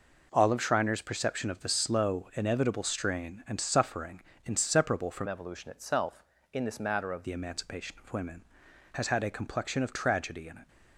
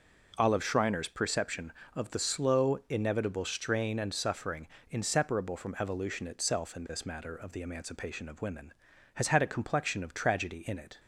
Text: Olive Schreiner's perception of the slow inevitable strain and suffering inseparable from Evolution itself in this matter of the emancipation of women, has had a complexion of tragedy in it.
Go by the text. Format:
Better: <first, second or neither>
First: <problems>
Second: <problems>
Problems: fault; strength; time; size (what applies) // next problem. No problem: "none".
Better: second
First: pauses between "suffering" and "inseparable"; slight; at 4.2 s; 0.24 s long // changes voice from "Evolution" to "of"; from 5.2 to 7.2 s; 2.0 s long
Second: pauses between "suffering" and "inseparable"; slight; at 4.6 s; 0.22 s long